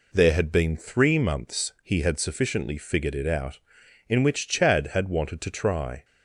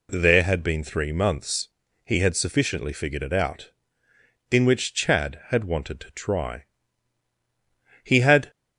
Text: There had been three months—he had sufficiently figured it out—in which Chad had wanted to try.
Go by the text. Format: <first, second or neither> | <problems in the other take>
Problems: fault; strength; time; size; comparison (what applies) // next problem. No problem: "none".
first | goes on to say "He had"; slight; from 8.0 s on; 0.48 s long